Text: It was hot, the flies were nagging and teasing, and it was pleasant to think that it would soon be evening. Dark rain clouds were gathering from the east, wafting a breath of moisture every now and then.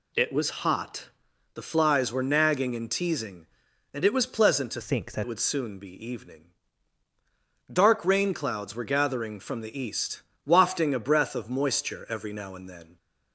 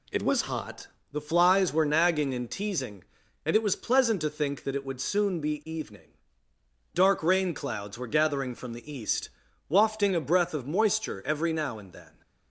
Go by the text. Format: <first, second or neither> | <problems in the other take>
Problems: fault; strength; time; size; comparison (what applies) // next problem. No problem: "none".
second | changes voice from "think" to "that"; from 4.8 to 5.2 s; 0.4 s long